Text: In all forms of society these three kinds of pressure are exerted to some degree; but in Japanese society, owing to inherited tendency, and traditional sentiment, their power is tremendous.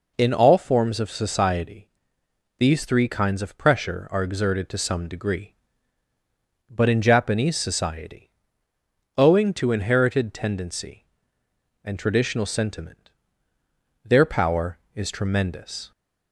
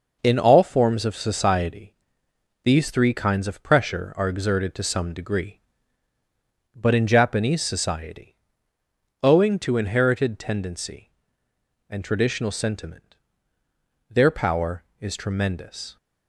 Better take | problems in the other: first | gets quieter; throughout; 7 dB // pauses between "society" and "these"; noticeable; at 1.9 s; 0.70 s long; noticeable in the first

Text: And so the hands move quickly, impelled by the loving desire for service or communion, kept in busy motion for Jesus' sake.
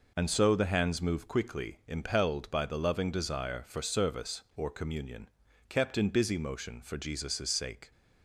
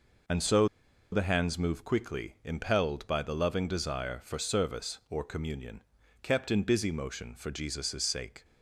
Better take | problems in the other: first | pauses between "so" and "the"; noticeable; at 0.6 s; 0.46 s long

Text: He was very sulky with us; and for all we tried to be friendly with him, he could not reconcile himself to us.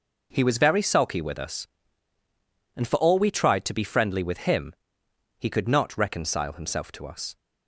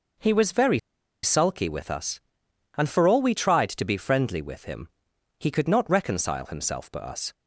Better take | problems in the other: first | pauses between "very" and "sulky"; at 0.7 s; 0.44 s long

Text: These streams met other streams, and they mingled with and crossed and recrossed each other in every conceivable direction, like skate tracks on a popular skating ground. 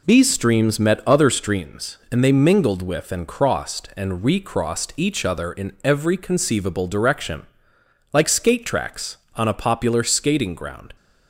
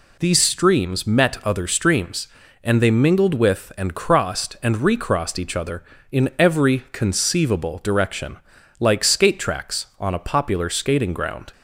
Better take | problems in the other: neither | none

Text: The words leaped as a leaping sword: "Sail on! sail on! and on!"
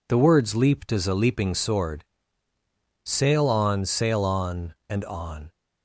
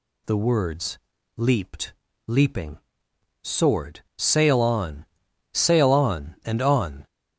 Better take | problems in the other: first | pauses between "words" and "leaped"; at 0.9 s; 0.38 s long // skips "as a"; at 2.0 s // pauses between "leaping" and "sword"; noticeable; at 2.7 s; 0.64 s long

